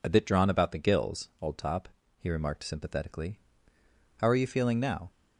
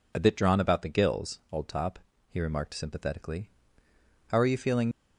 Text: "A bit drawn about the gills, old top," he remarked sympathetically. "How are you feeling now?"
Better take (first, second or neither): first